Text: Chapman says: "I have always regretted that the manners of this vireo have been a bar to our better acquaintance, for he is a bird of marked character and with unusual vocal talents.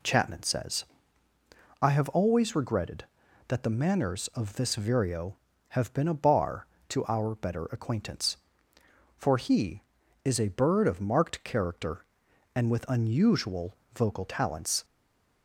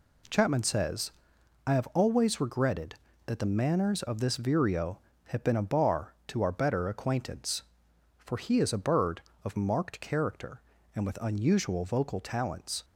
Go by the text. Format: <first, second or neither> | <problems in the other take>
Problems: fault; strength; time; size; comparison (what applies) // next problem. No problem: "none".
second | pauses between "unusual" and "vocal"; slight; at 13.7 s; 0.18 s long // stays silent after the last word; slight; from 14.8 s on; 0.6 s long